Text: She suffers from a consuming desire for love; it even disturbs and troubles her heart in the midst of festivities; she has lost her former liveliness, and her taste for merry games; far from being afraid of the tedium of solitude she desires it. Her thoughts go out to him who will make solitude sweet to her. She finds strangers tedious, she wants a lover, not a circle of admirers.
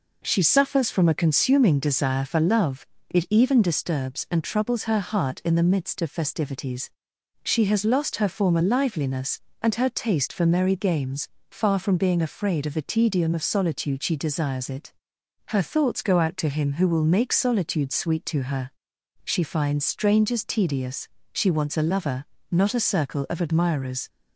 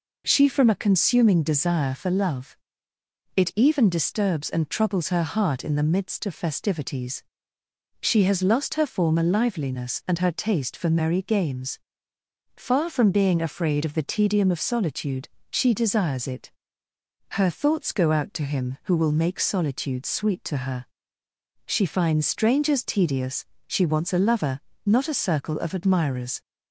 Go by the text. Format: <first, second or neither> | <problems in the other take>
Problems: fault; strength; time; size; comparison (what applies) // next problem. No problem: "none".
first | skips "suffers"; at 0.4 s // pauses between "solitude" and "she"; slight; at 15.2 s; 0.22 s long